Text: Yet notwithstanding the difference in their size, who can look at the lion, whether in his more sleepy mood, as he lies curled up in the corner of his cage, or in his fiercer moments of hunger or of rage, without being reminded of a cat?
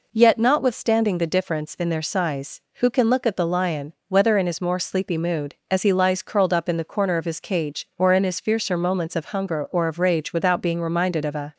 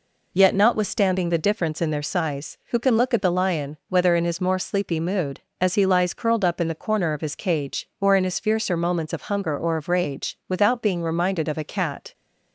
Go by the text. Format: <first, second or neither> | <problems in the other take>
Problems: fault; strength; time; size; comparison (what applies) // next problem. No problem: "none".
second | stops before "cat"; at 11.5 s